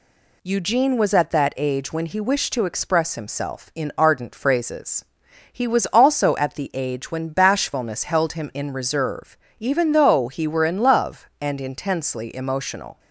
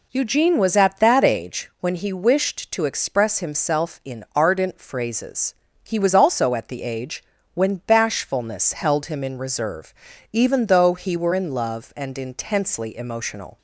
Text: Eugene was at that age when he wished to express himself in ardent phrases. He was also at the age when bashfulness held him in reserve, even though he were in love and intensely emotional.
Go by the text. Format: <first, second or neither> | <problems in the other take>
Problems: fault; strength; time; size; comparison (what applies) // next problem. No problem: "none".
first | starts louder than the rest; until 1.7 s; 3.5 dB // pauses between "age" and "when"; slight; at 7.2 s; 0.30 s long